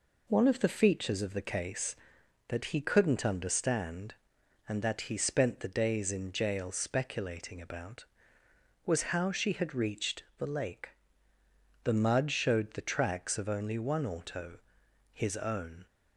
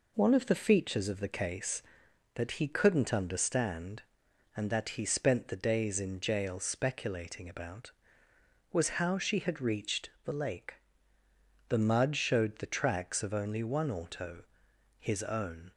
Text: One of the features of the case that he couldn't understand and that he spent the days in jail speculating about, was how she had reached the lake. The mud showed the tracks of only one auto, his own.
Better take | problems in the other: neither | pauses between "reached" and "the"; slight; the same in both

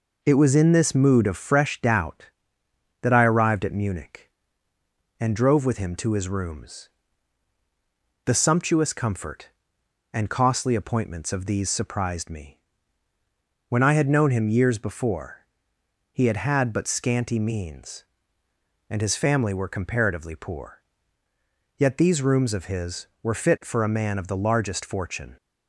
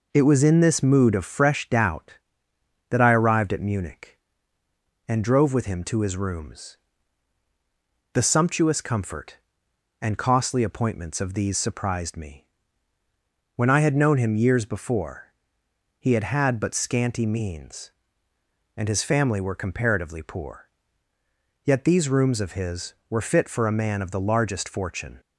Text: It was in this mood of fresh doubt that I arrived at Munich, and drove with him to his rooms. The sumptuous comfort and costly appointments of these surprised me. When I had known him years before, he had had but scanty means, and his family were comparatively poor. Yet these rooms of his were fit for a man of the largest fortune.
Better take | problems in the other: neither | none

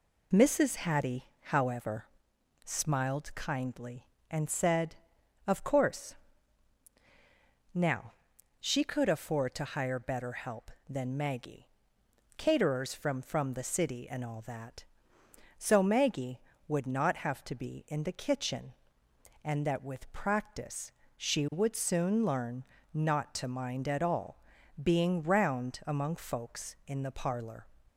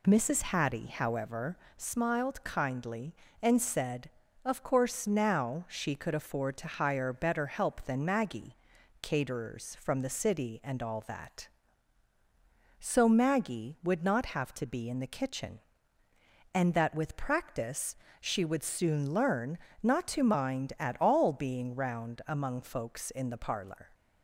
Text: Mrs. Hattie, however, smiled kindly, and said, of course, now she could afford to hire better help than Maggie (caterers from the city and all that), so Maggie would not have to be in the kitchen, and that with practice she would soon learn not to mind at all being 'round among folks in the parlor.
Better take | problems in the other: second | pauses between "now" and "she"; noticeable; at 8.1 s; 0.46 s long // says "from" twice; at 13.1 s // pauses between "practice" and "she"; slight; at 20.9 s; 0.26 s long; slight in the second // pauses between "learn" and "not"; slight; at 22.6 s; 0.28 s long; slight in the second // pauses between "all" and "being"; at 24.4 s; 0.40 s long

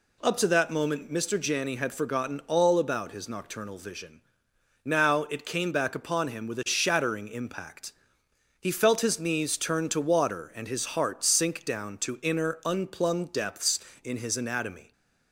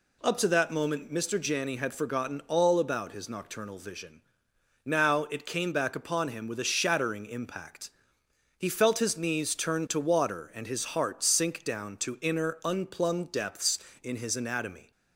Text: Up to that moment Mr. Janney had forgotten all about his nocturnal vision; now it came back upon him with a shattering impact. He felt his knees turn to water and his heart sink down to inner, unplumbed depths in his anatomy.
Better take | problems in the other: neither | none

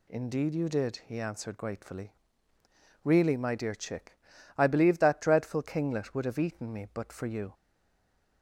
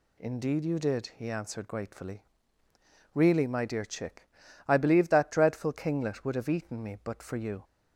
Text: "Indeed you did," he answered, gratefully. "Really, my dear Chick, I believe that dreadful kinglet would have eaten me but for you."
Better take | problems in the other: second | stays silent after the last word; slight; from 7.5 s on; 0.9 s long

